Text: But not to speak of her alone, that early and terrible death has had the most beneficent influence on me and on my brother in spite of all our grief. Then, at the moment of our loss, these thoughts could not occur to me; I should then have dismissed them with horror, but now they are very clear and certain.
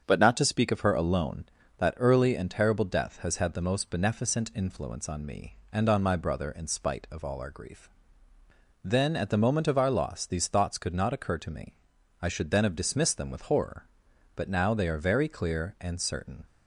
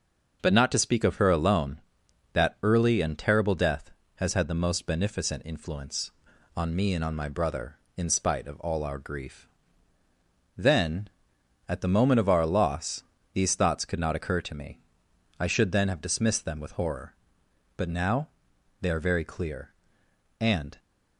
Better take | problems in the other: first | starts louder than the rest; noticeable; until 1.4 s; 6 dB; strong in the first // pauses between "now" and "they"; noticeable; at 18.2 s; 0.50 s long // stops before "certain"; at 20.7 s

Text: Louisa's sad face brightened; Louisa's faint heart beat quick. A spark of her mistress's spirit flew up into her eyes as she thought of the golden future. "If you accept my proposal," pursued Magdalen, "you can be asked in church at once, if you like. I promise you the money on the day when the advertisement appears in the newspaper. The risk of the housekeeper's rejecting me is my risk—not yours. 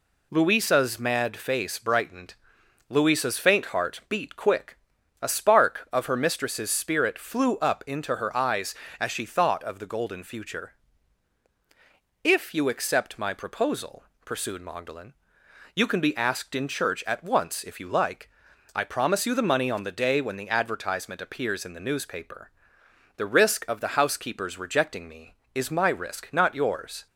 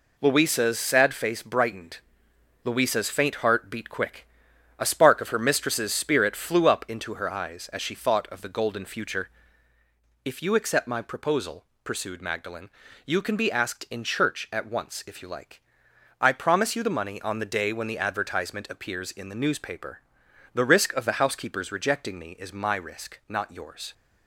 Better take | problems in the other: second | says "mad" for "sad"; at 0.9 s

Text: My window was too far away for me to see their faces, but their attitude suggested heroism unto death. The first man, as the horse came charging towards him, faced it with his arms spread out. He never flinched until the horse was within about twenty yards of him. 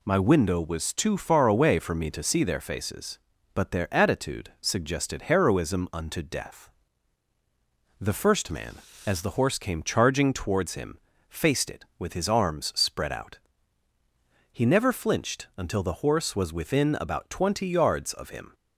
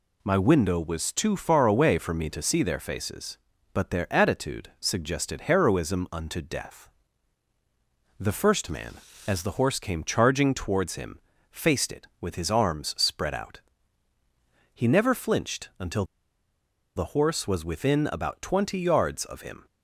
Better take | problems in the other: first | pauses between "until" and "the"; noticeable; at 16.0 s; 0.92 s long

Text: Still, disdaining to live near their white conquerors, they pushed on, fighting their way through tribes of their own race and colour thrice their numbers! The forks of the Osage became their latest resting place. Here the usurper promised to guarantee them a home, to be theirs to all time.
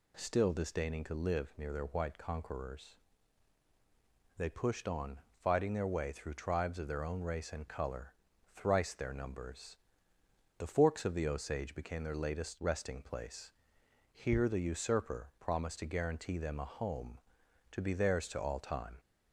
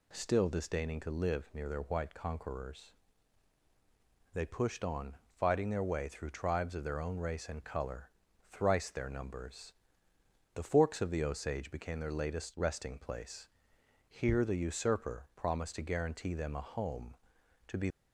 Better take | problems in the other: first | pauses between "colour" and "thrice"; at 8.0 s; 0.42 s long; also in the first // stops before "theirs to all time"; at 17.8 s

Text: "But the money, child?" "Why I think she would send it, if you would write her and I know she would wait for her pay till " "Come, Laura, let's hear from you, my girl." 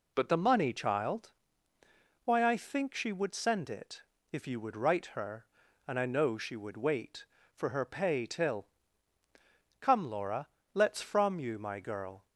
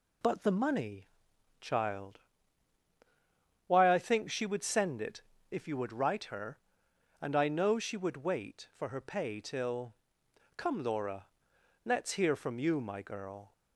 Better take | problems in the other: second | skips "hear"; at 11.0 s

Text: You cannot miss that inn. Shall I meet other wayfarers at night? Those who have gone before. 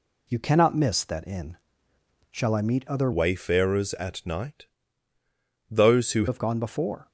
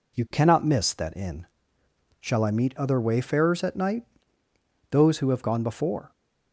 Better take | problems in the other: second | changes voice from "wayfarers" to "who"; from 3.1 to 6.2 s; 3.1 s long

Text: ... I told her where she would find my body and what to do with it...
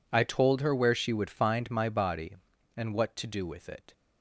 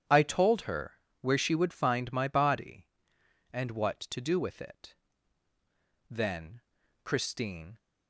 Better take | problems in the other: first | starts louder than the rest; strong; until 1.2 s; 9.5 dB // pauses between "her" and "where"; slight; at 1.0 s; 0.18 s long // goes on to say "Then Christine"; strong; from 6.0 s on; 1.6 s long

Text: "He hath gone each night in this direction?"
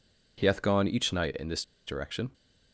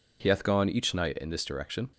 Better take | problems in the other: second | pauses between "this" and "direction"; slight; at 1.6 s; 0.22 s long

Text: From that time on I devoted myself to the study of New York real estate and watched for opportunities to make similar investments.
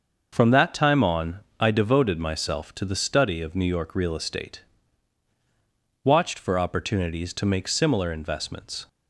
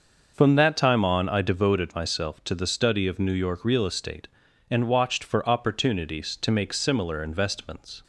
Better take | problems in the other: second | starts louder than the rest; until 1.3 s; 6.5 dB; noticeable in the second // pauses between "on" and "I"; slight; at 1.4 s; 0.16 s long // skips "and"; at 5.3 s

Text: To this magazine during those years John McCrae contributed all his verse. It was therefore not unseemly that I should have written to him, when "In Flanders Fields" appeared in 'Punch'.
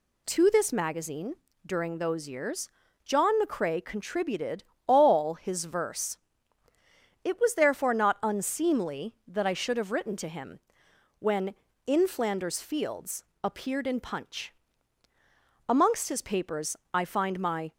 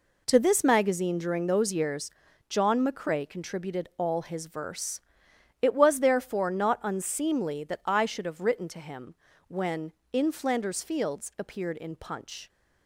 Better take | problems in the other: second | pauses between "magazine" and "during"; slight; at 1.3 s; 0.30 s long // pauses between "years" and "John"; slight; at 2.6 s; 0.36 s long; also in the second // pauses between "contributed" and "all"; slight; at 4.6 s; 0.24 s long // pauses between "Fields" and "appeared"; slight; at 13.2 s; 0.20 s long // goes on to say "Amongst his papers I find my"; strong; from 15.6 s on; 2.0 s long

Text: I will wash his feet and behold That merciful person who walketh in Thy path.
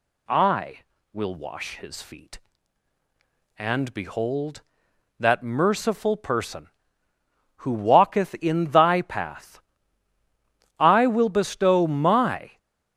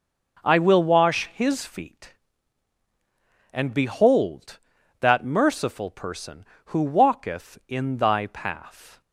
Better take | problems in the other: second | goes on to say "I will bestow my"; strong; from 10.7 s on; 1.8 s long

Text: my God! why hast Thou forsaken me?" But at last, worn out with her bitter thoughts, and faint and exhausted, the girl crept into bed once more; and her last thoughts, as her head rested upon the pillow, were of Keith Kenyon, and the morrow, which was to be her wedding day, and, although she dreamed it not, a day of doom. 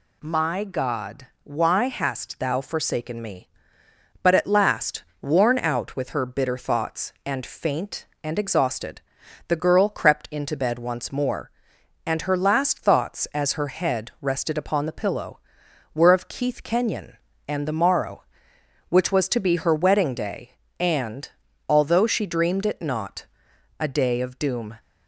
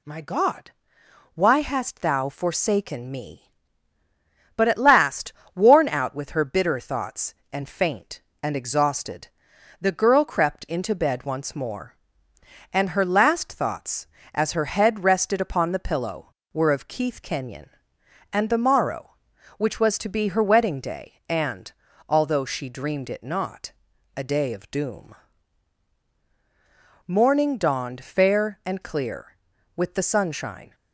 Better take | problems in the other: first | goes on to say "Morning dawned fair and clear with the sunshine"; strong; from 27.0 s on; 3.6 s long

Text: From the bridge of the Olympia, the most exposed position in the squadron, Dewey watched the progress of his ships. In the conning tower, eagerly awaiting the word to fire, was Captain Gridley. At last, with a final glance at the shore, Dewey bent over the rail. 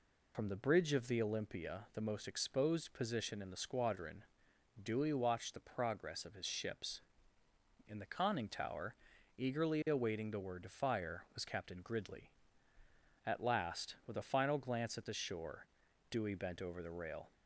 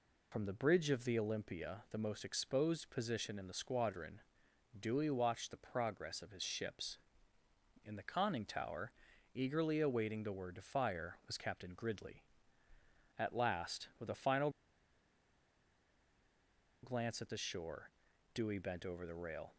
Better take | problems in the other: first | pauses between "final" and "glance"; strong; at 14.4 s; 2.3 s long

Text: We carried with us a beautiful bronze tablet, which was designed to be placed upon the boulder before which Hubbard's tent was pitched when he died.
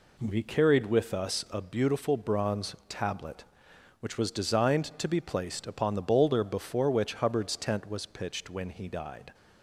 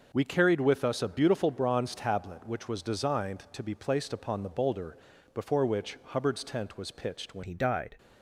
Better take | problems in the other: first | pauses between "boulder" and "before"; slight; at 4.9 s; 0.34 s long // changes voice at "he"; from 7.4 s on; 0.5 s long

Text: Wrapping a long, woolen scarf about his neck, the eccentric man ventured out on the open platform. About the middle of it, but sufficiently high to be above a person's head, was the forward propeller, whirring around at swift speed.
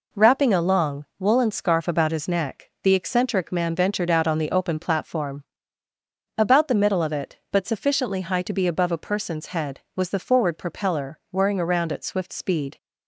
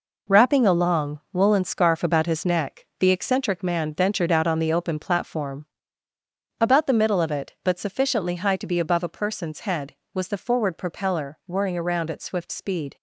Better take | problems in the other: first | gets quieter; strong; throughout; 8.5 dB

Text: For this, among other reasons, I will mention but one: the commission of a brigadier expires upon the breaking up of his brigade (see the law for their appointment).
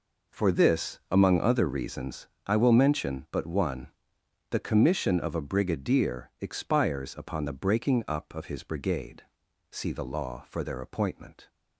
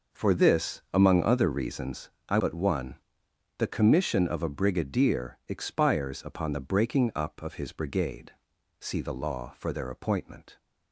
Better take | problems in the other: first | skips "will mention"; at 2.3 s

